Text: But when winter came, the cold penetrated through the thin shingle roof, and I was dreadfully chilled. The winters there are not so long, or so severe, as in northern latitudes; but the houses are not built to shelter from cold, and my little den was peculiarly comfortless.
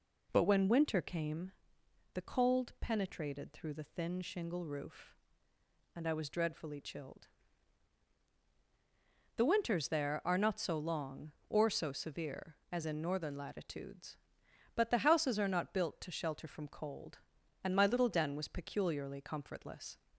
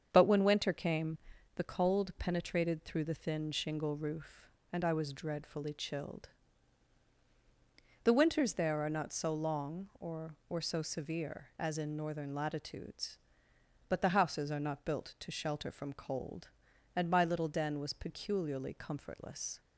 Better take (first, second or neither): first